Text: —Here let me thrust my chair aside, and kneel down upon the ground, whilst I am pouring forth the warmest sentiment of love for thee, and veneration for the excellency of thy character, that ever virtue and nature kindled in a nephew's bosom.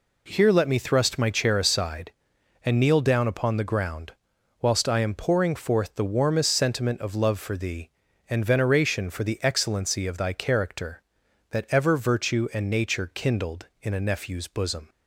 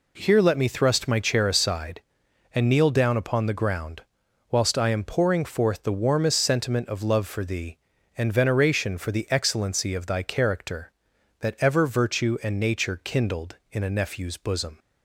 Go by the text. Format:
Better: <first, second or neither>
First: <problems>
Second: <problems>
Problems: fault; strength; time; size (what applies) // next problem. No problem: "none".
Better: neither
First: none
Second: none